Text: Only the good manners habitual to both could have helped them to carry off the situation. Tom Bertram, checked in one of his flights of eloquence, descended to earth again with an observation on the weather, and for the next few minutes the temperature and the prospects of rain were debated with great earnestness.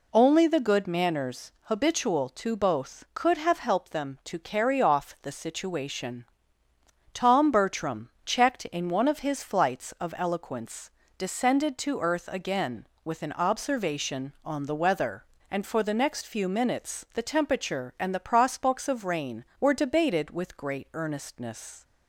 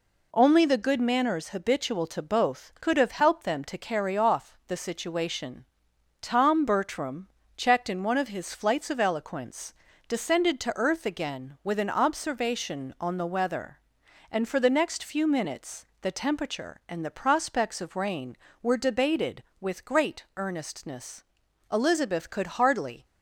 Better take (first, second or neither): first